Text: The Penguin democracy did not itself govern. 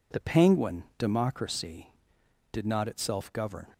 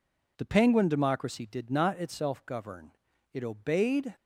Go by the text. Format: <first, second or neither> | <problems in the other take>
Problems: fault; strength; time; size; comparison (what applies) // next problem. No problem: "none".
first | goes on to say "It obeyed"; noticeable; from 3.3 s on; 0.82 s long